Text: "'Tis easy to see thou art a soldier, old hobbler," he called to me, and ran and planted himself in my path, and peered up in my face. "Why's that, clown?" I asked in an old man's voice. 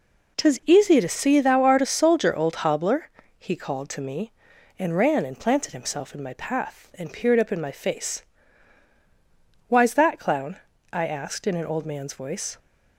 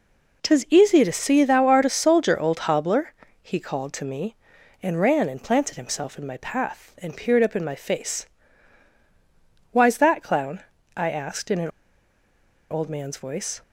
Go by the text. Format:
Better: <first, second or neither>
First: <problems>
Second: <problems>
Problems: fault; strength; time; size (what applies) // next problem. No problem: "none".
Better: first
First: none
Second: pauses between "an" and "old"; at 11.6 s; 1.0 s long